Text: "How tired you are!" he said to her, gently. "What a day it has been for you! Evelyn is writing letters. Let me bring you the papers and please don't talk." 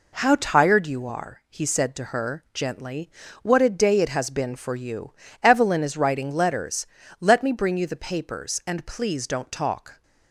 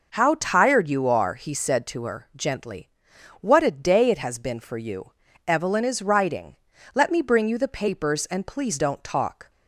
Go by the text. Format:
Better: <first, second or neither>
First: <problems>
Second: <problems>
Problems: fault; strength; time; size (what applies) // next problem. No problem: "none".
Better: first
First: none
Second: skips "letters"; at 6.7 s